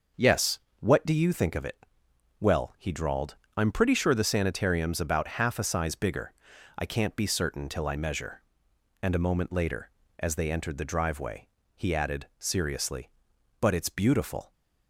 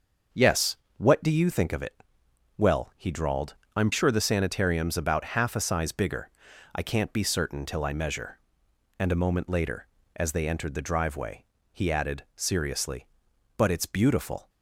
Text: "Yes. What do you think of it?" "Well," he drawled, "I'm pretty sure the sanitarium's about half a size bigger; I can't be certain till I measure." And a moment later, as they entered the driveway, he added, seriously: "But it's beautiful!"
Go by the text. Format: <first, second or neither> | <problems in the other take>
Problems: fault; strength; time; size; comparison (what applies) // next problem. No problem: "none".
first | starts louder than the rest; until 1.5 s; 6.5 dB; noticeable in the first // skips "pretty"; at 3.9 s